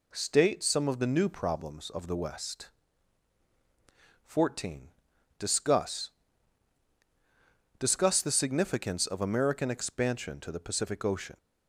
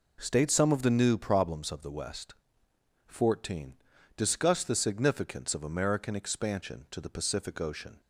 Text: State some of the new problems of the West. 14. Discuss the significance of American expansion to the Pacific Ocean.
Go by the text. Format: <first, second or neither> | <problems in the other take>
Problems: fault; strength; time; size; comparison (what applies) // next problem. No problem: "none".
second | says "Discuss" twice; at 7.7 s